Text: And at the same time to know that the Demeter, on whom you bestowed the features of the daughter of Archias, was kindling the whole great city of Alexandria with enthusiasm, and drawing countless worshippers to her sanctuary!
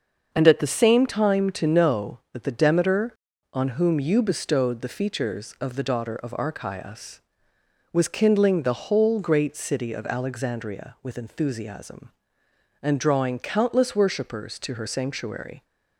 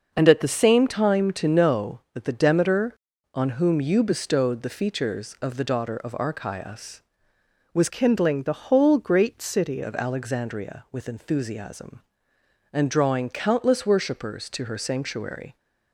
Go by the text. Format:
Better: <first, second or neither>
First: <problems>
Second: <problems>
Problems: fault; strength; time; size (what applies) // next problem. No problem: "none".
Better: first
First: starts louder than the rest; until 1.3 s; 6.5 dB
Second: starts louder than the rest; until 1.1 s; 6 dB // changes voice from "kindling" to "city"; from 7.8 to 9.8 s; 2.0 s long